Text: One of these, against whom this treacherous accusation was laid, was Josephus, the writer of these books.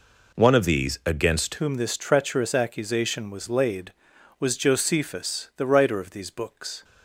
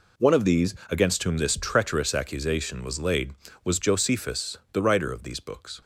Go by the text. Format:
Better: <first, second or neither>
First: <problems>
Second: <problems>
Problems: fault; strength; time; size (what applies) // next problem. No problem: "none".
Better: second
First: changes voice at "whom"; from 1.5 s on; 5.3 s long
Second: none